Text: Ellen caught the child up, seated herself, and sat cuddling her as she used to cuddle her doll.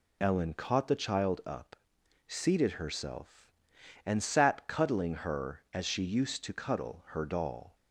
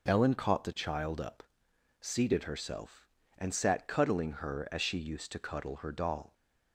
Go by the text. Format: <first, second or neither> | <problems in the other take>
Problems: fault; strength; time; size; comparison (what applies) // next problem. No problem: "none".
neither | none